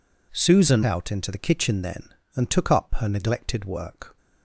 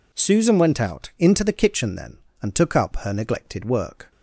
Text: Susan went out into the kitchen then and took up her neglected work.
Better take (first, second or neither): second